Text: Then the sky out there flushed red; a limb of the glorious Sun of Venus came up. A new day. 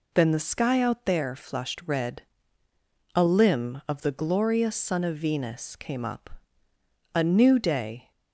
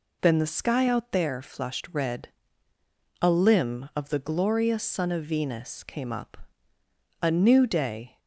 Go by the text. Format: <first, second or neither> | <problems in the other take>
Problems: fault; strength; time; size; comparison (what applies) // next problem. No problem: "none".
neither | none